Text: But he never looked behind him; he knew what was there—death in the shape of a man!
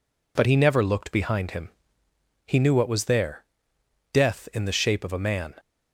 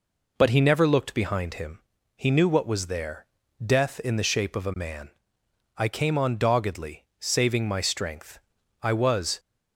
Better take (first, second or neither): first